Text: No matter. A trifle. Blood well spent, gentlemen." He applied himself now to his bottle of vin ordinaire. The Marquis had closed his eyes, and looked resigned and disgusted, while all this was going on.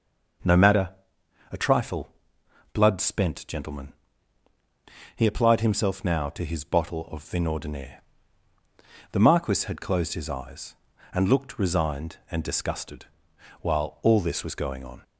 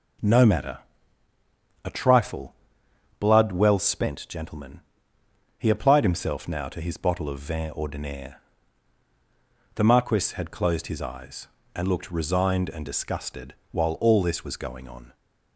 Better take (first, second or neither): second